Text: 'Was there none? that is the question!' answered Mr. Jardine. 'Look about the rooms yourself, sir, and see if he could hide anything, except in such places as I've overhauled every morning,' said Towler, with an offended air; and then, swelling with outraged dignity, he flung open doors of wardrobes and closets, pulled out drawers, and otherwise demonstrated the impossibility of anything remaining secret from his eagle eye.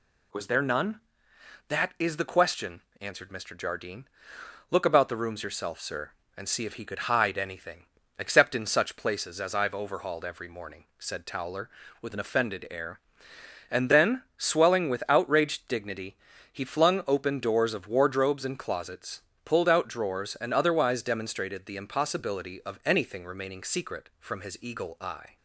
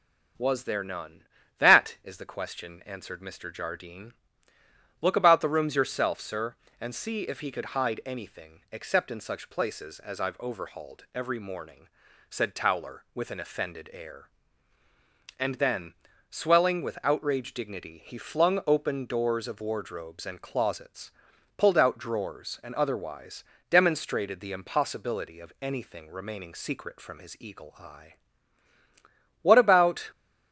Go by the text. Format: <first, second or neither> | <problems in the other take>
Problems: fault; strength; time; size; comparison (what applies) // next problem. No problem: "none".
first | starts louder than the rest; noticeable; until 1.7 s; 6 dB // pauses between "otherwise" and "demonstrated"; slight; at 23.4 s; 0.24 s long // goes on to say "What about"; noticeable; from 29.4 s on; 0.68 s long